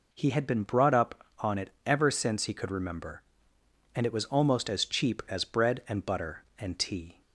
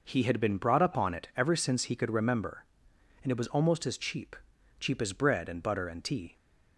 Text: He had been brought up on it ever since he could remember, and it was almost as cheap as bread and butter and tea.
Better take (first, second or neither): first